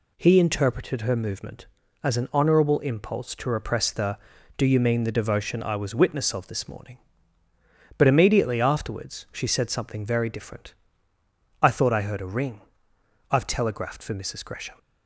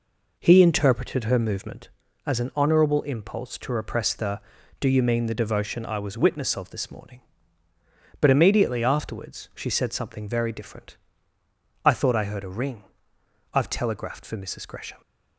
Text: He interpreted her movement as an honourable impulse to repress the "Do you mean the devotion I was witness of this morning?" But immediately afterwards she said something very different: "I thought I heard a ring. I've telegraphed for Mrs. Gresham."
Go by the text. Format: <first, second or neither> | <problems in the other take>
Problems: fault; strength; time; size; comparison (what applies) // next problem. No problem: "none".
first | starts louder than the rest; noticeable; until 1.8 s; 4.5 dB